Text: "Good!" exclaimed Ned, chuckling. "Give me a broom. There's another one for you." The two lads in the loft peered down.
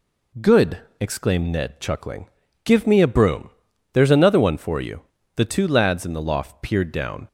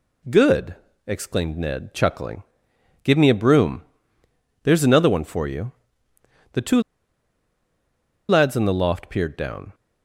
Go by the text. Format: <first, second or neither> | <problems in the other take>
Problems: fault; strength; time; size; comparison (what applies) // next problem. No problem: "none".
first | pauses between "two" and "lads"; strong; at 6.7 s; 1.4 s long